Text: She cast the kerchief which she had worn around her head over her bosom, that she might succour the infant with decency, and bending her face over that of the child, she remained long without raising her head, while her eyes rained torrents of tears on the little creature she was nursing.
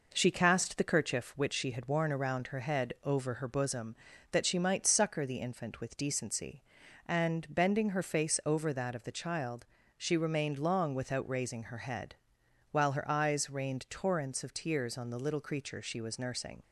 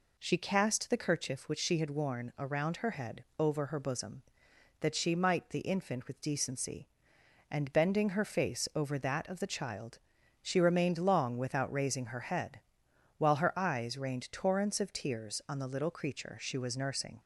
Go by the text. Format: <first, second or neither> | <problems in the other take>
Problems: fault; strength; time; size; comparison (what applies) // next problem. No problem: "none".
first | skips "succour"; at 5.5 s